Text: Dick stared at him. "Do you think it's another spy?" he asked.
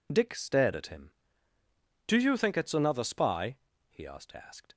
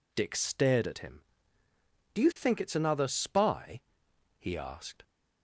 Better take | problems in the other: second | says "asked" twice; at 4.3 s

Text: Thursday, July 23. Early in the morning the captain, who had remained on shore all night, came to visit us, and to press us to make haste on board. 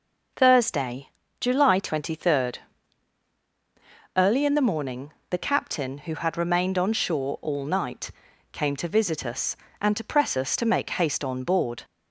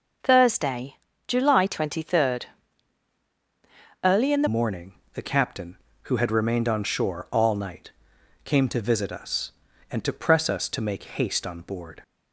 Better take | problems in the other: first | changes voice at "morning"; from 4.4 s on; 7.6 s long // pauses between "morning" and "the"; slight; at 4.9 s; 0.22 s long; slight in the first

